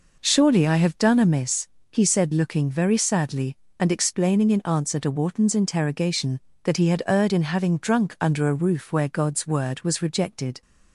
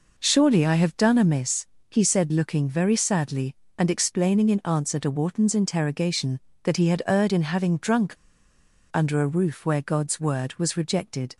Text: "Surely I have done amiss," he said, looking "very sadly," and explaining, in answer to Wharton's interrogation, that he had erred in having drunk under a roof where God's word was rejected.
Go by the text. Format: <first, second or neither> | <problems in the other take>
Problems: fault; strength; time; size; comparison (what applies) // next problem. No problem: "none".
first | pauses between "drunk" and "under"; noticeable; at 8.1 s; 0.75 s long